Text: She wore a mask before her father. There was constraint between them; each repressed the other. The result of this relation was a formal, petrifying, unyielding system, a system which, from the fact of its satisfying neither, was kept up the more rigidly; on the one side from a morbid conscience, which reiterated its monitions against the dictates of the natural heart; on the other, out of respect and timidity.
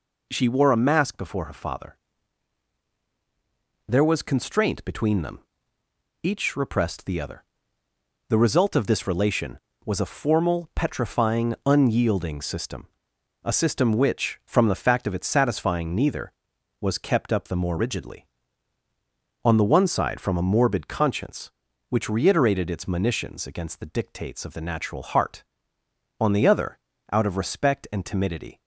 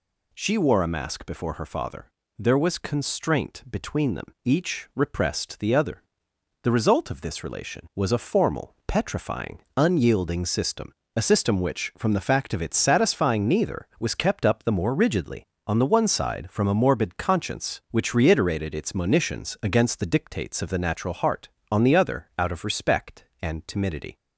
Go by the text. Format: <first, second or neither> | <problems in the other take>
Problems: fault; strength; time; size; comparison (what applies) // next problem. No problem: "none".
neither | none